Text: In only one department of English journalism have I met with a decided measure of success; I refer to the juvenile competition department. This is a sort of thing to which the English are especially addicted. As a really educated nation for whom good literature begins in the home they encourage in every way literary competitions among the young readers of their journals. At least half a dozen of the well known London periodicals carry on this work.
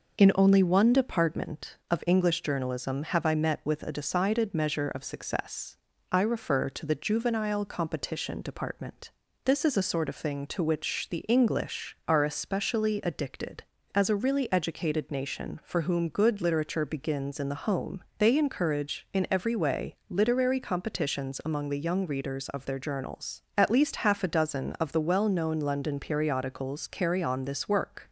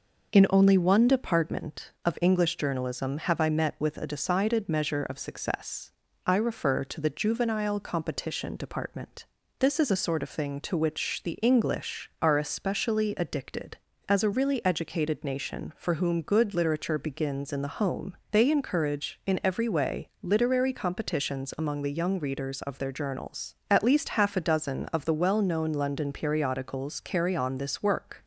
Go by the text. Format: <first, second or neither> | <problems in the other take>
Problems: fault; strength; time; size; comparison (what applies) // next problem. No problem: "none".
neither | pauses between "home" and "they"; slight; the same in both